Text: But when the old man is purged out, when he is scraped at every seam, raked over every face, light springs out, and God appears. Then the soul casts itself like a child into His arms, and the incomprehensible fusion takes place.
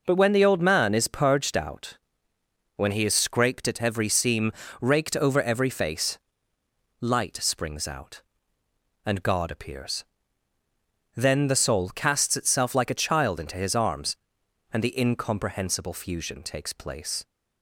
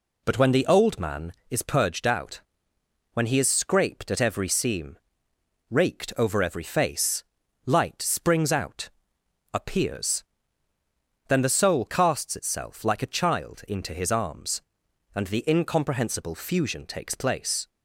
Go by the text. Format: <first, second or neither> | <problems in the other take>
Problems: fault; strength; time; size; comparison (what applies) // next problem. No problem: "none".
first | skips "and God"; at 9.2 s